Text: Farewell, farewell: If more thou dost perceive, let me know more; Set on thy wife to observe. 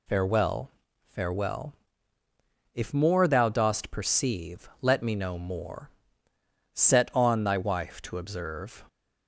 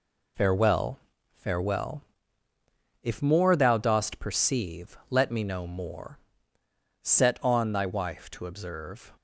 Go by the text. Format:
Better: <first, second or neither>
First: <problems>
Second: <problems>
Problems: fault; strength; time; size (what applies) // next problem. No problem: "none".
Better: first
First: none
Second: gets quieter; throughout; 6.5 dB